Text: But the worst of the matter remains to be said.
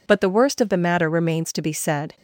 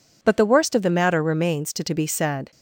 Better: first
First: none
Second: says "to" twice; at 1.8 s

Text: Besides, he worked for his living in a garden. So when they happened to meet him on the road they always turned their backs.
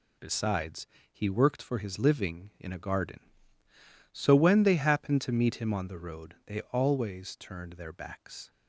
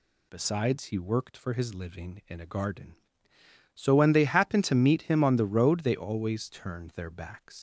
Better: first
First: none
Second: leaves "backs" unfinished; at 7.5 s; 50 ms

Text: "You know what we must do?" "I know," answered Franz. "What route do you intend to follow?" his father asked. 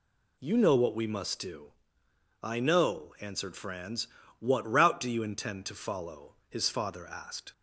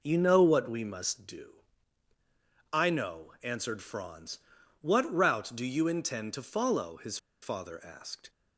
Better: first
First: none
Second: pauses between "his" and "father"; slight; at 7.1 s; 0.25 s long

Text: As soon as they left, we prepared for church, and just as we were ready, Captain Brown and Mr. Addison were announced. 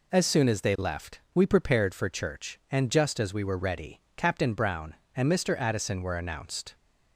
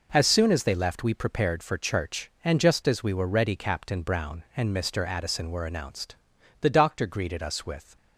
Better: first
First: none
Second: goes on to say "The Doctor greeted us with"; from 6.6 s on; 1.3 s long

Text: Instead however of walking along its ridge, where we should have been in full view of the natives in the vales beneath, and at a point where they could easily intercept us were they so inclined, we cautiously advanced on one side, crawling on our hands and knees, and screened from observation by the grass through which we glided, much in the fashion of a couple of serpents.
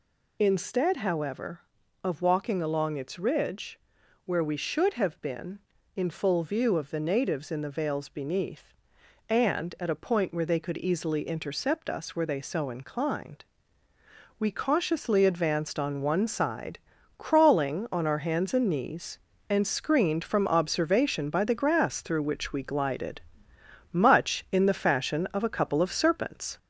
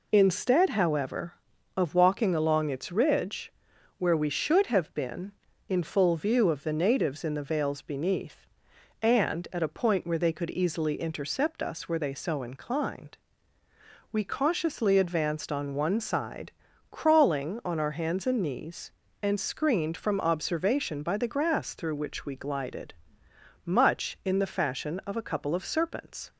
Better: second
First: gets louder; slight; throughout; 3 dB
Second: none

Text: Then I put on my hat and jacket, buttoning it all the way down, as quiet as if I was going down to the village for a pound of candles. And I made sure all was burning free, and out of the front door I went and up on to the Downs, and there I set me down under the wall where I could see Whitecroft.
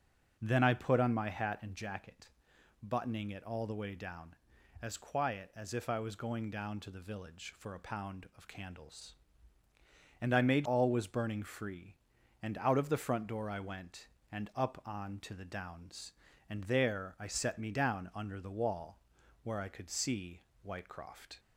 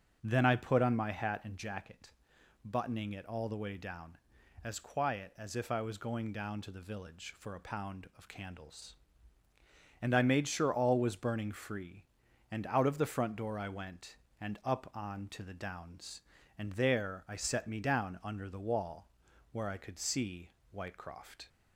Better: second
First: starts louder than the rest; until 1.4 s; 6.5 dB // skips "sure"; at 10.6 s // pauses between "wall" and "where"; at 18.9 s; 0.44 s long // pauses between "see" and "Whitecroft"; slight; at 20.4 s; 0.22 s long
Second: starts louder than the rest; until 1.2 s; 6.5 dB // pauses between "wall" and "where"; at 19.0 s; 0.44 s long // pauses between "see" and "Whitecroft"; slight; at 20.5 s; 0.22 s long

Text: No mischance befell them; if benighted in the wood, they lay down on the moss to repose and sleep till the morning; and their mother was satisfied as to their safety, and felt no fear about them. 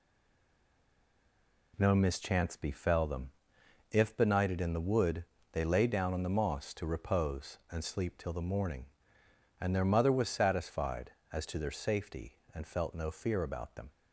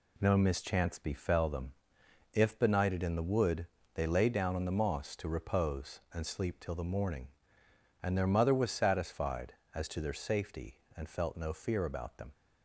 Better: second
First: stays silent before the first word; noticeable; until 1.7 s; 1.7 s long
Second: none

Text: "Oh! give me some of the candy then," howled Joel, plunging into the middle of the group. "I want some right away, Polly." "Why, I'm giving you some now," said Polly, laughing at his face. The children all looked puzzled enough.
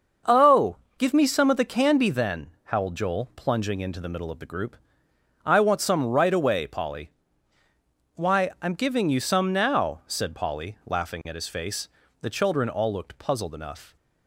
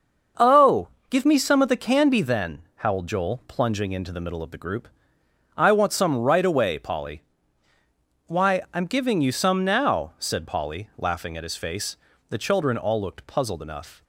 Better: neither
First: starts louder than the rest; until 1.4 s; 6.5 dB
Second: starts louder than the rest; until 1.6 s; 6.5 dB

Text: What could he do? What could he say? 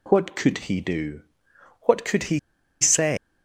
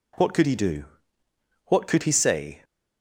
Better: second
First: pauses between "he" and "say"; at 2.3 s; 0.42 s long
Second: none

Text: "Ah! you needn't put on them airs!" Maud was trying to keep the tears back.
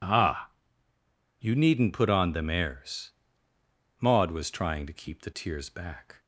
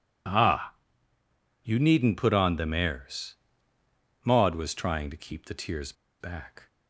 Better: first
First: none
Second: pauses between "tears" and "back"; slight; at 5.9 s; 0.27 s long

